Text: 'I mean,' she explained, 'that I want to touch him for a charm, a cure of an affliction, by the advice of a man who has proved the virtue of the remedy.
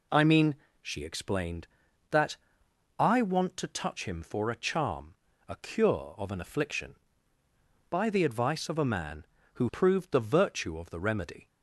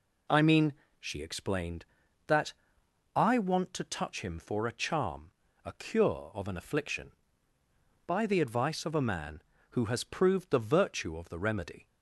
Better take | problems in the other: second | pauses between "that" and "I"; noticeable; at 2.3 s; 0.60 s long; noticeable in the second // skips "has"; at 9.6 s

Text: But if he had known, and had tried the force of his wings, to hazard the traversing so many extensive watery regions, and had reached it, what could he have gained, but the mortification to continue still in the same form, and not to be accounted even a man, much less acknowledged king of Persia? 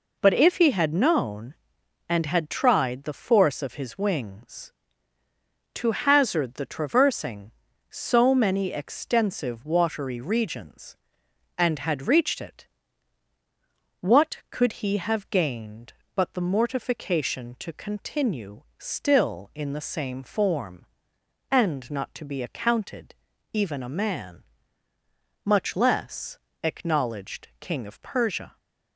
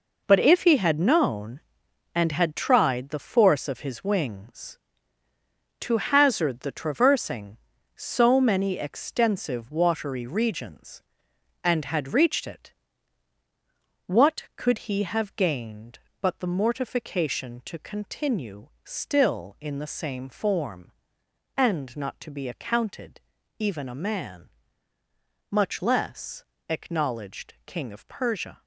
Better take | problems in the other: first | gets quieter; strong; throughout; 9.5 dB // pauses between "continue" and "still"; slight; at 18.6 s; 0.16 s long; slight in the first // pauses between "accounted" and "even"; at 23.1 s; 0.40 s long; also in the first // pauses between "less" and "acknowledged"; slight; at 26.4 s; 0.24 s long; slight in the first

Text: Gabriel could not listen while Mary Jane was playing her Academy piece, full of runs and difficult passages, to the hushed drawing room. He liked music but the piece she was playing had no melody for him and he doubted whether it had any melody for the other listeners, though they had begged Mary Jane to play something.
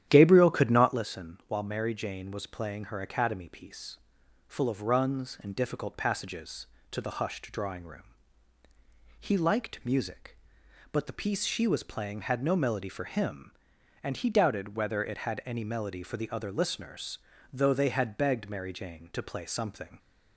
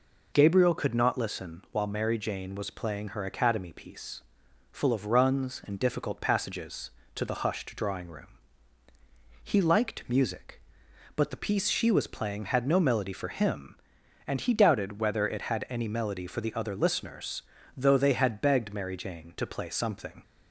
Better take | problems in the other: second | starts louder than the rest; strong; until 1.0 s; 10.5 dB

